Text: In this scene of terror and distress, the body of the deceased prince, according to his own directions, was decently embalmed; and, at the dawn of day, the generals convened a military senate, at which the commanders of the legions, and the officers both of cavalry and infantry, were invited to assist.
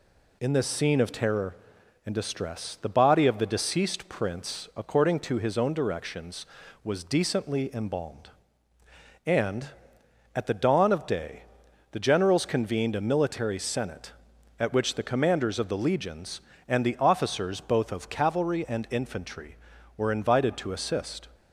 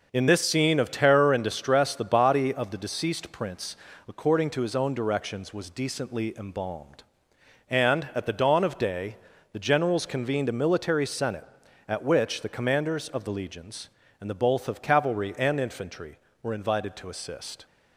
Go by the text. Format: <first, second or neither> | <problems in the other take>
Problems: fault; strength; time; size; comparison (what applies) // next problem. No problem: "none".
first | skips "officers"; at 14.3 s